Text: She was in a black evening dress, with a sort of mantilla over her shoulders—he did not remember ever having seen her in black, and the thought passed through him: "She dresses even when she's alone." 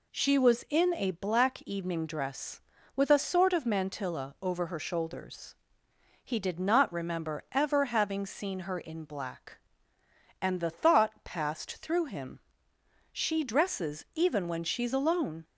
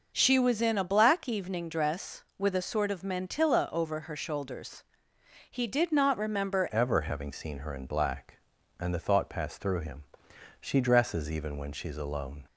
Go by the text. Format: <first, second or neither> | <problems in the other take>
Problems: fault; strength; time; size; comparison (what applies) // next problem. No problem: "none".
first | changes voice at "ever"; from 6.7 s on; 5.7 s long